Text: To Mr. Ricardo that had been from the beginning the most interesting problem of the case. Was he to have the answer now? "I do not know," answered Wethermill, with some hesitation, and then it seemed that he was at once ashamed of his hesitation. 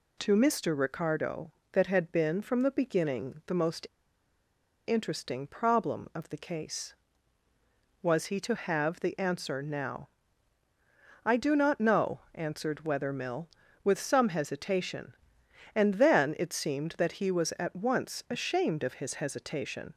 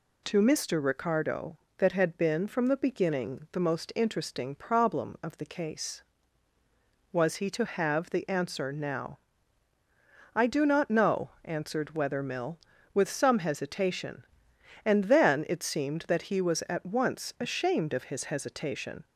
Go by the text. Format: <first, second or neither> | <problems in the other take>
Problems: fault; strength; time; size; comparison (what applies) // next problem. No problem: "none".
second | pauses between "most" and "interesting"; at 3.8 s; 0.99 s long